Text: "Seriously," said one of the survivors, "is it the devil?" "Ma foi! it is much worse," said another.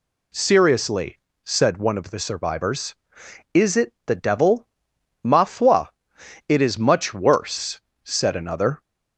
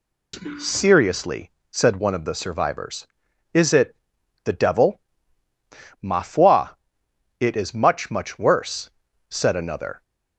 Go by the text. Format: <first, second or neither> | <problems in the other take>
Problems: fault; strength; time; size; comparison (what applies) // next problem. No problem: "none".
first | pauses between "it" and "the"; noticeable; at 3.9 s; 0.48 s long // says "much" twice; at 8.1 s